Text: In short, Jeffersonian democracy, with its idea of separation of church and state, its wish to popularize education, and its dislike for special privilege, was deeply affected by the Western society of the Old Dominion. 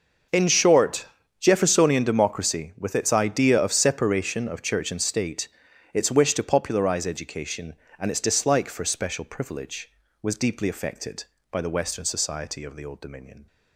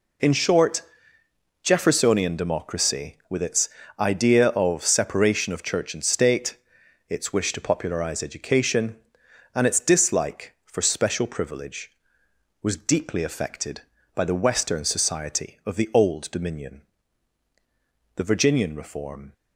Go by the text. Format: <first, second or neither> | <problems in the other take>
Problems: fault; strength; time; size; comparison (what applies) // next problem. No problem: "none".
first | pauses between "its" and "idea"; slight; at 3.6 s; 0.30 s long // goes on to say "The Virginian reform"; noticeable; from 18.1 s on; 1.1 s long